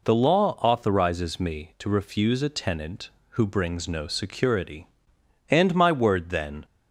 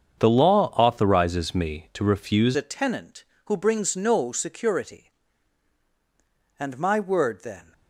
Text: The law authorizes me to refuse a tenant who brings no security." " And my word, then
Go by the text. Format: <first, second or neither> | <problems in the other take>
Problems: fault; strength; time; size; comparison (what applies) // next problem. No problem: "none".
first | starts louder than the rest; strong; until 1.2 s; 8 dB // changes voice at "a"; from 2.5 s on; 5.2 s long